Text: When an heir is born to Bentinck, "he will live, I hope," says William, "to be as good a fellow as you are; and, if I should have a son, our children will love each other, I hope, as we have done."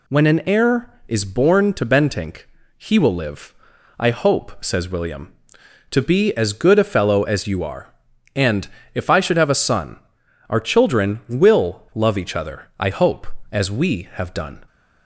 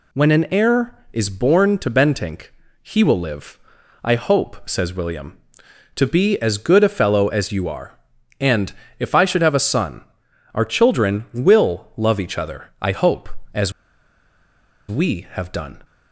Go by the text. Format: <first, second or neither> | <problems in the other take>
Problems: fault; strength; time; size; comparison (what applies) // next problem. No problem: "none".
first | pauses between "as" and "we"; at 13.7 s; 1.1 s long